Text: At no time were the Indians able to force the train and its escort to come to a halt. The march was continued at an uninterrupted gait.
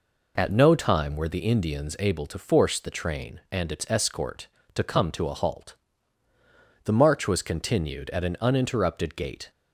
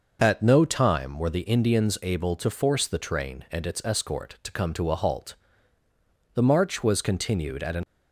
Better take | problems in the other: first | stops before "uninterrupted gait"; at 7.8 s

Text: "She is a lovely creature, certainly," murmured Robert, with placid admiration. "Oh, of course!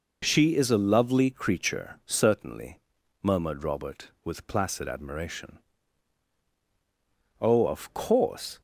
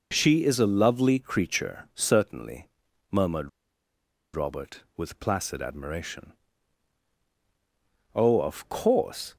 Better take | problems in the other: first | pauses between "murmured" and "Robert"; noticeable; at 3.4 s; 0.84 s long

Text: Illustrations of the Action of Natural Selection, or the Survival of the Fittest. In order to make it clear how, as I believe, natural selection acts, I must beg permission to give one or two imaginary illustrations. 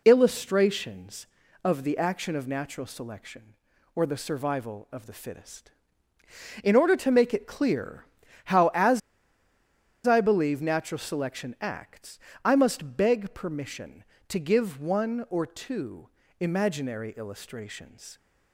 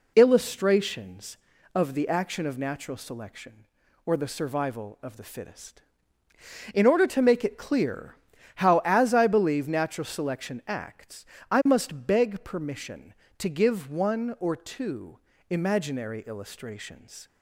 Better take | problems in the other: second | pauses between "clear" and "how"; at 8.0 s; 0.40 s long; also in the second // pauses between "as" and "I"; at 9.0 s; 1.0 s long // pauses between "two" and "imaginary"; slight; at 16.0 s; 0.30 s long; slight in the second

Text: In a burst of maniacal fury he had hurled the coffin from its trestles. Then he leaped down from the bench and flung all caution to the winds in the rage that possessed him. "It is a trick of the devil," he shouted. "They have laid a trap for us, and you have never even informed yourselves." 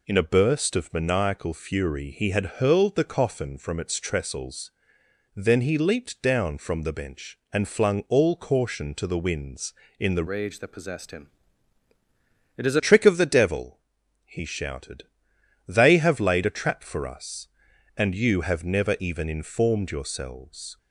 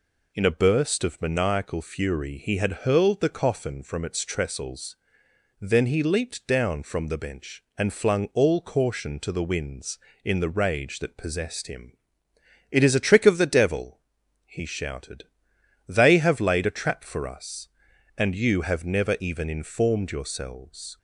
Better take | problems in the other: second | changes voice from "rage" to "is"; from 10.2 to 12.7 s; 2.5 s long

